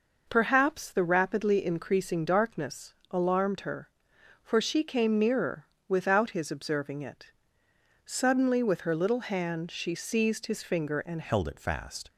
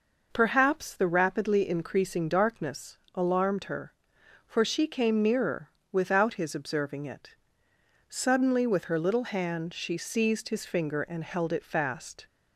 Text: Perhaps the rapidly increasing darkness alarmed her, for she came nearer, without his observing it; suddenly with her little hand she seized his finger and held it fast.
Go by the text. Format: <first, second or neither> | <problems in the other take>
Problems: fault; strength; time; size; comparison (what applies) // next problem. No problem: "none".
second | pauses between "darkness" and "alarmed"; slight; at 2.9 s; 0.18 s long; slight in the second // changes voice at "held"; from 11.2 s on; 0.8 s long